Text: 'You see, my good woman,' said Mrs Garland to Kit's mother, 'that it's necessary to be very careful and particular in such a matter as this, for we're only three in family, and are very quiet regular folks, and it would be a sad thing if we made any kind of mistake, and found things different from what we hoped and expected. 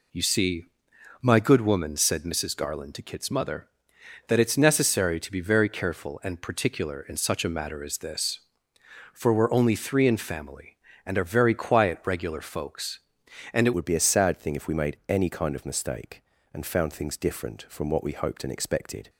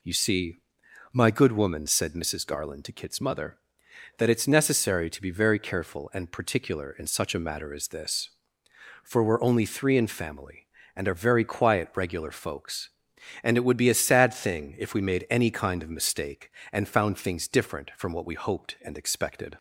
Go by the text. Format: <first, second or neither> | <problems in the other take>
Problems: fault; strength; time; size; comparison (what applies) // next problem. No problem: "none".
second | changes voice at "would"; from 13.7 s on; 5.3 s long